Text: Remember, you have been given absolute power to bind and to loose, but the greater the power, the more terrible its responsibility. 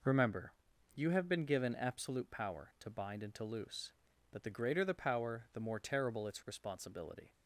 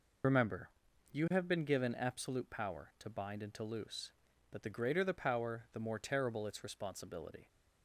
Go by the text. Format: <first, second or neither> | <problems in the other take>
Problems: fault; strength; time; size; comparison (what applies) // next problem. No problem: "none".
first | loses the start of "Remember"; at 0.2 s; 45 ms